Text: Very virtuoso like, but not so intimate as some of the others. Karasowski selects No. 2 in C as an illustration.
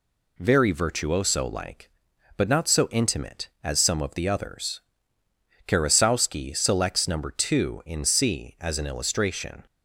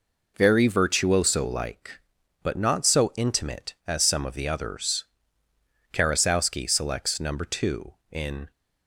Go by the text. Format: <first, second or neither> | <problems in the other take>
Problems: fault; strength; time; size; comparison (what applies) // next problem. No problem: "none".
first | stops before "C as an illustration"; at 8.5 s